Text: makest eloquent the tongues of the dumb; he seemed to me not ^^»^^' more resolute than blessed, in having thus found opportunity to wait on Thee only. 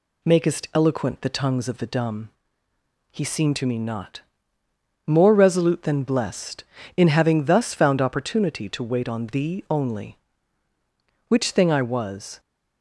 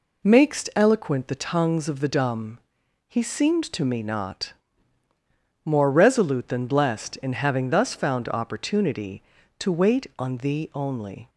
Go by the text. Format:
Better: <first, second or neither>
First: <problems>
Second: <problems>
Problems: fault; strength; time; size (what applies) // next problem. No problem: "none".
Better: second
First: goes on to say "Which thing I was"; noticeable; from 11.2 s on; 1.1 s long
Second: none